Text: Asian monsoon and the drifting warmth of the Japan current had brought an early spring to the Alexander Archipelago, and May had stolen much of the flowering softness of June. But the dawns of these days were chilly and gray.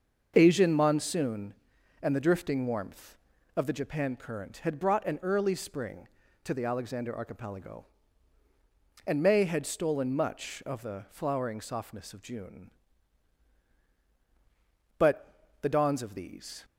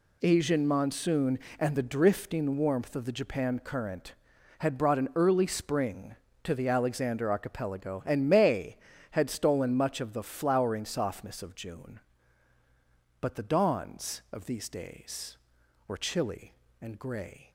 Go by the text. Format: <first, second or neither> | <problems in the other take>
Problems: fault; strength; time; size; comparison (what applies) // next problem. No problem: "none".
second | starts louder than the rest; until 1.3 s; 6.5 dB // pauses between "But" and "the"; slight; at 15.2 s; 0.34 s long // stops before "days were chilly and gray"; at 16.6 s